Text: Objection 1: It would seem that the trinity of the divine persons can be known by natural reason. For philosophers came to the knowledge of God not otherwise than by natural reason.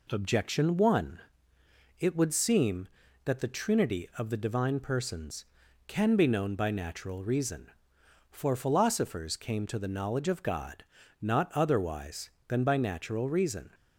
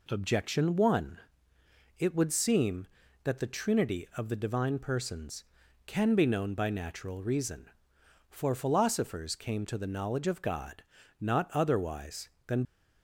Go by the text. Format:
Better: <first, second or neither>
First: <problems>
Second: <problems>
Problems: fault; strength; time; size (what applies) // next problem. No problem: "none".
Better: first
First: pauses between "God" and "not"; slight; at 10.8 s; 0.36 s long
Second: pauses between "God" and "not"; slight; at 10.8 s; 0.36 s long // stops before "by natural reason"; at 12.6 s